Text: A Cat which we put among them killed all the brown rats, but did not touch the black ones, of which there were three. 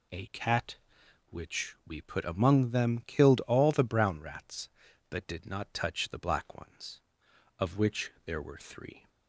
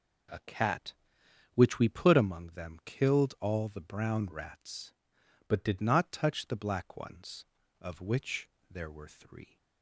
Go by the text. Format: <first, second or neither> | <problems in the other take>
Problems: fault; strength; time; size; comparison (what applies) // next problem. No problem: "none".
first | changes voice from "but" to "did"; from 5.4 to 5.7 s; 0.3 s long // pauses between "which" and "there"; slight; at 8.4 s; 0.22 s long